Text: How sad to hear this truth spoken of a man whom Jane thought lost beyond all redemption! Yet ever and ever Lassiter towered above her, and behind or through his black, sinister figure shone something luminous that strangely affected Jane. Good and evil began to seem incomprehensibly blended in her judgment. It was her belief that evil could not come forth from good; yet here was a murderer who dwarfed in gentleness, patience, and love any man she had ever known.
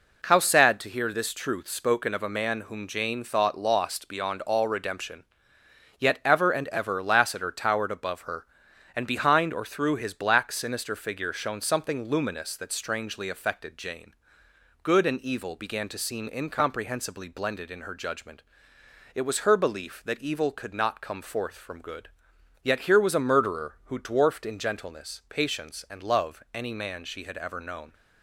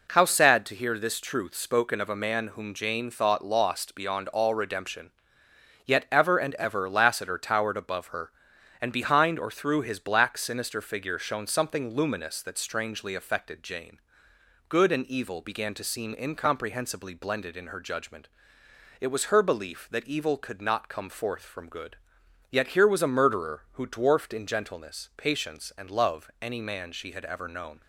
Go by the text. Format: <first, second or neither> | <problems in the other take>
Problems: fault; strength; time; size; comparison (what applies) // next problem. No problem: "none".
neither | none